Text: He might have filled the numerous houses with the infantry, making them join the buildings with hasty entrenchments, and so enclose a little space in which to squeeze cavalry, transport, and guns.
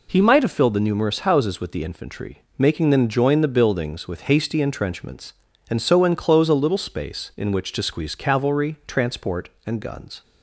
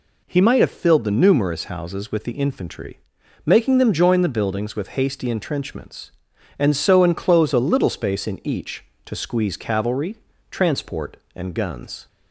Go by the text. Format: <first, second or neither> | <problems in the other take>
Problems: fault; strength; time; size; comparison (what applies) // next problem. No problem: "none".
first | says "each" for "which"; at 8.4 s